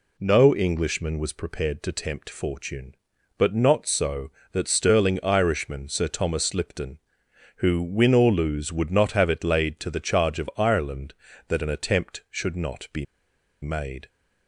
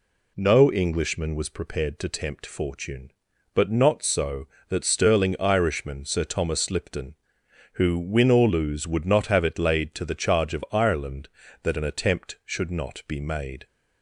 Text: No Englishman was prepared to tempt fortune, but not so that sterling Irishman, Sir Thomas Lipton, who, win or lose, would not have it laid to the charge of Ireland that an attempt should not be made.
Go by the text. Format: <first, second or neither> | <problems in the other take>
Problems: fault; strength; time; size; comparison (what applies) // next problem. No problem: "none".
second | pauses between "be" and "made"; noticeable; at 13.0 s; 0.56 s long